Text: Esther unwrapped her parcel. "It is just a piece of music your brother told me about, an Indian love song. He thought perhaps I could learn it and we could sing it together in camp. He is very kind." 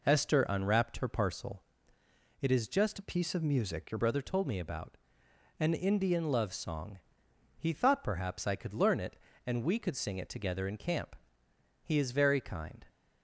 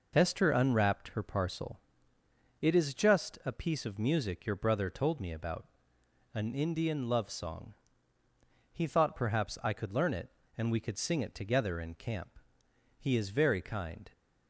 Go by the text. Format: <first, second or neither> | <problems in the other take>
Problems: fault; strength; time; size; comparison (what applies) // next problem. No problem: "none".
second | changes voice from "a" to "your"; from 2.9 to 3.9 s; 1.0 s long